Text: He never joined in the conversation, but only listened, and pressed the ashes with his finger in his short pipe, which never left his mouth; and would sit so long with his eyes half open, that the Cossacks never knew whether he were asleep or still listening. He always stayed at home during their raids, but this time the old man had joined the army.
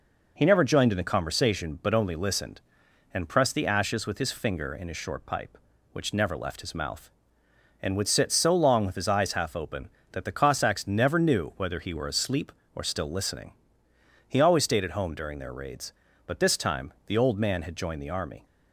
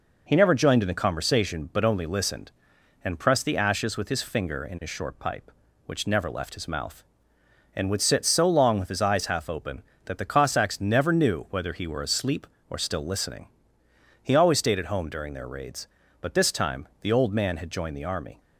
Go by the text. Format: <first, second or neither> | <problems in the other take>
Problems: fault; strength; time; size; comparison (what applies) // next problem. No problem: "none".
neither | pauses between "time" and "the"; slight; the same in both